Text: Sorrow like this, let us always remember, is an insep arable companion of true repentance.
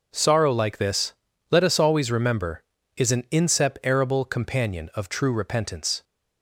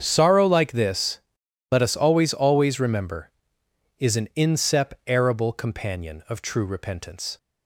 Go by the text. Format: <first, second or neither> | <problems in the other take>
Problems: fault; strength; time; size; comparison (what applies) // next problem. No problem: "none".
first | starts louder than the rest; strong; until 1.0 s; 7.5 dB // says "always" twice; at 2.3 s